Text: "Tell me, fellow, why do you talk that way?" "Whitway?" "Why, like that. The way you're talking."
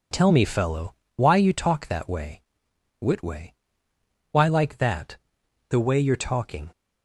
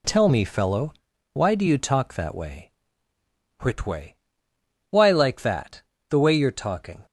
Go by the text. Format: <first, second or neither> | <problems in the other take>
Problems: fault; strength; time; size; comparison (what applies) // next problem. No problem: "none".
second | skips "do"; at 1.3 s